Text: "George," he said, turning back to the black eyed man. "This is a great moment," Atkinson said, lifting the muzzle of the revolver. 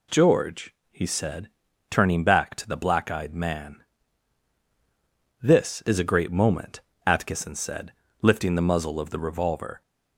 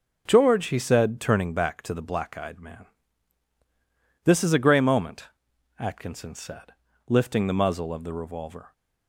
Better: first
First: none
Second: says "grey" for "great"; at 4.5 s

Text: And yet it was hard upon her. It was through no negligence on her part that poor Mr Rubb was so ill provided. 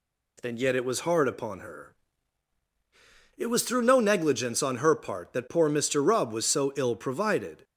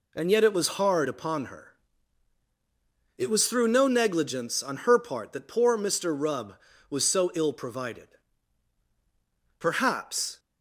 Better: first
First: none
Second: goes on to say "Perhaps"; noticeable; from 9.5 s on; 0.80 s long

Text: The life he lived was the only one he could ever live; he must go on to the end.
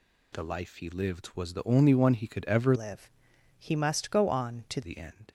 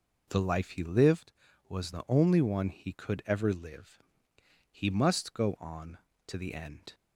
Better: second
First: changes voice from "live" to "to"; from 2.7 to 4.8 s; 2.1 s long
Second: none

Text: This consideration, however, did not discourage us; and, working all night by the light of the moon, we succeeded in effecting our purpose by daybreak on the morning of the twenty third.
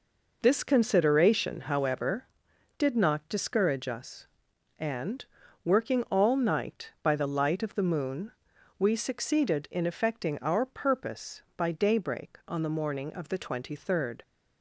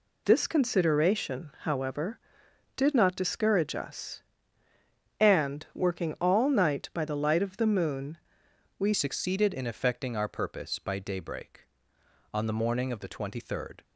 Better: first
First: none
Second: changes voice at "succeeded"; from 8.9 s on; 4.9 s long

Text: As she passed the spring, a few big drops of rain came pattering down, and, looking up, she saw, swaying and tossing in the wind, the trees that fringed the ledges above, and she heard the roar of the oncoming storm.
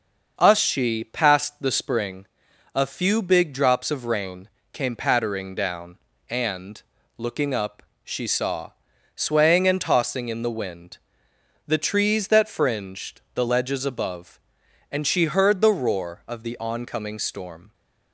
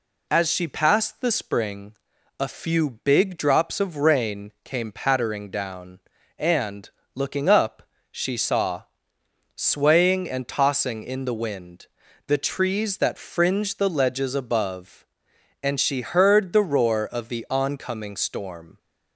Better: second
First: starts louder than the rest; until 1.3 s; 6 dB // says "Us" for "As"; at 0.3 s // pauses between "rain" and "came"; slight; at 4.4 s; 0.24 s long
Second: none

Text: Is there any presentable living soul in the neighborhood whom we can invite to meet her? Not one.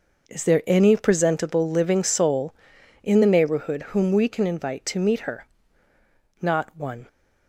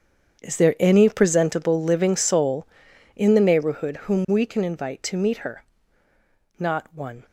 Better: first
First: none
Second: gets quieter; strong; throughout; 16.5 dB

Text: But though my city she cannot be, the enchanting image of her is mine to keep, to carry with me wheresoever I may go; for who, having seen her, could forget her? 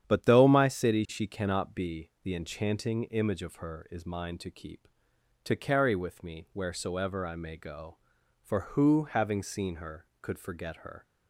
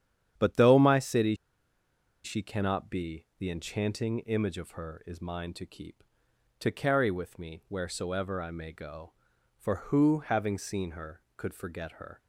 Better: first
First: starts louder than the rest; strong; until 1.1 s; 9 dB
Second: starts louder than the rest; strong; until 2.2 s; 9 dB // pauses between "city" and "she"; noticeable; at 1.3 s; 0.90 s long

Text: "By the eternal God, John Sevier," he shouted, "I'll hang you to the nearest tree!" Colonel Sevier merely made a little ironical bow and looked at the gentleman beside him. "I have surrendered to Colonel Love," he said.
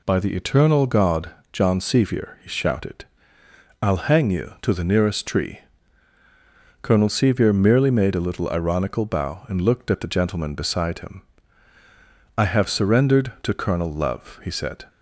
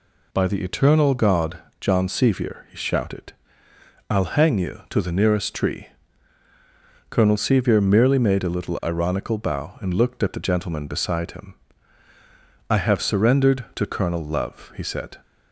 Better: neither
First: none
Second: none

